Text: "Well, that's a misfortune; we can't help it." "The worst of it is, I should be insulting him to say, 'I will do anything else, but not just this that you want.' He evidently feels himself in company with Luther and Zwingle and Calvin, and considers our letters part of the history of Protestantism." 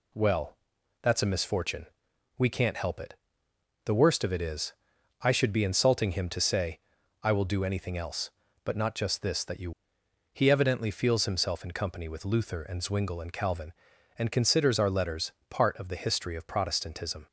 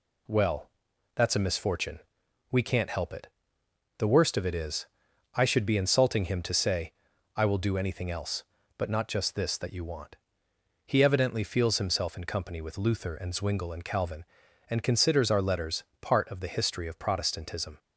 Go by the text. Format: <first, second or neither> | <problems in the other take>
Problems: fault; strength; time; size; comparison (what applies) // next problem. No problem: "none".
second | skips "want"; at 10.0 s // pauses between "letters" and "part"; slight; at 15.3 s; 0.18 s long; slight in the second